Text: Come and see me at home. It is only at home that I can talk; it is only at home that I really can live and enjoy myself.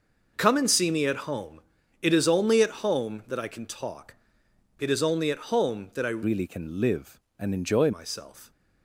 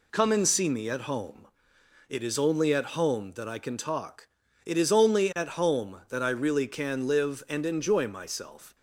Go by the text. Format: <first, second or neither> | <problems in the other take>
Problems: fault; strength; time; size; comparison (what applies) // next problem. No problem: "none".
second | changes voice from "really" to "enjoy"; from 6.2 to 7.9 s; 1.7 s long